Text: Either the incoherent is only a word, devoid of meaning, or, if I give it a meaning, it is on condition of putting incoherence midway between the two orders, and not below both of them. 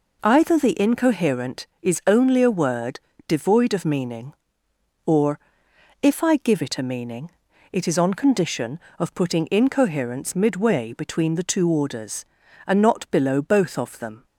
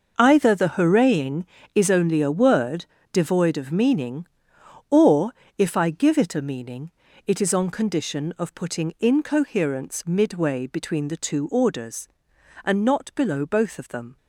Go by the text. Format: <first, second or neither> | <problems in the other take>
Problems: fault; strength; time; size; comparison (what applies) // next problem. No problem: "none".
first | starts louder than the rest; noticeable; until 1.1 s; 6 dB // says "hooraying" for "incoherent"; at 0.7 s